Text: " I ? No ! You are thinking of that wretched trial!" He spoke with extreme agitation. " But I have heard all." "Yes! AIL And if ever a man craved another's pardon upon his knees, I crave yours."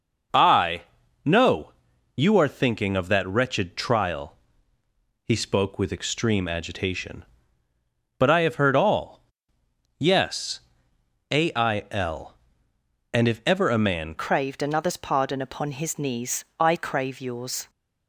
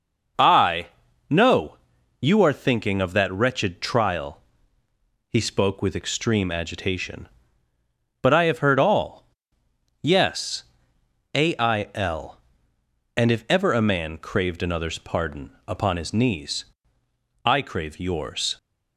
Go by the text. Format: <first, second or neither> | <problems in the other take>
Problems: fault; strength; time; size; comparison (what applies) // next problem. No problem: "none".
second | starts louder than the rest; noticeable; until 1.7 s; 6 dB; noticeable in the second // changes voice at "craved"; from 14.1 s on; 3.5 s long